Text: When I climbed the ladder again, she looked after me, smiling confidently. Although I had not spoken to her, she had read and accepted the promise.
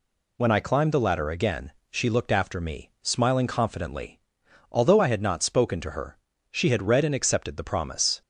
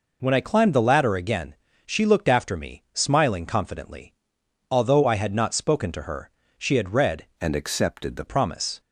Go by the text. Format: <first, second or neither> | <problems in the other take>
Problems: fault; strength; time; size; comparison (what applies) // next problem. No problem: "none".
first | changes voice from "and" to "the"; from 7.3 to 8.2 s; 0.9 s long